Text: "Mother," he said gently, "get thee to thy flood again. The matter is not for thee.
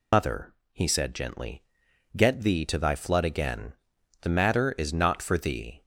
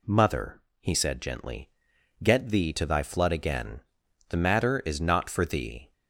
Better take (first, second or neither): second